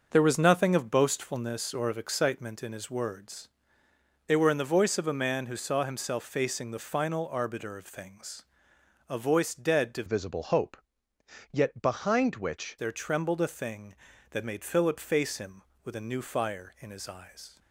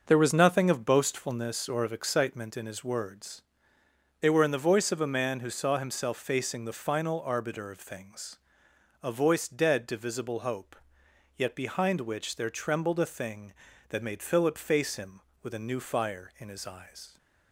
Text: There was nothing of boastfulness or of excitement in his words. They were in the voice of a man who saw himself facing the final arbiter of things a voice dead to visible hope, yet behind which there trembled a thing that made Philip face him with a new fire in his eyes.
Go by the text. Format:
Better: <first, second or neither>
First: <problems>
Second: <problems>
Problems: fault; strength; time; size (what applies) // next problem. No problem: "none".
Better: second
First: starts louder than the rest; until 1.1 s; 6.5 dB // pauses between "things" and "a"; noticeable; at 8.4 s; 0.66 s long // changes voice from "visible" to "which"; from 10.0 to 12.7 s; 2.7 s long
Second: starts louder than the rest; until 1.1 s; 6.5 dB // pauses between "things" and "a"; noticeable; at 8.3 s; 0.66 s long